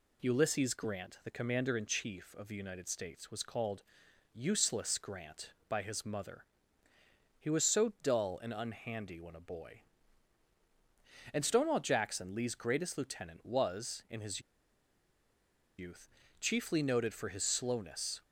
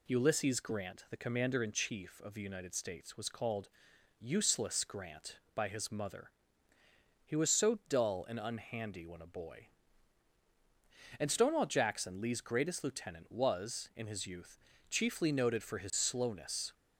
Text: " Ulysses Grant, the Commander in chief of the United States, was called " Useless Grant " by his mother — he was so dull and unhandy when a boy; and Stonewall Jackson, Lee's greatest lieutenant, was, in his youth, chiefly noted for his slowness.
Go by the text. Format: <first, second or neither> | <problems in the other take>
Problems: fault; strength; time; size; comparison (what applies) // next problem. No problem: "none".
second | pauses between "his" and "youth"; strong; at 14.4 s; 1.3 s long